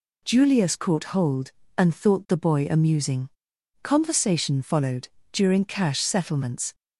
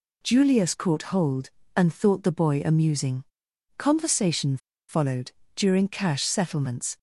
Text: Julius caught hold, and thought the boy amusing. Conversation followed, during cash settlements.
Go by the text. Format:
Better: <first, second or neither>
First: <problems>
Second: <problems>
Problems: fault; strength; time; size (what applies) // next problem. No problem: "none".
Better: first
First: none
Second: pauses between "Conversation" and "followed"; slight; at 4.5 s; 0.31 s long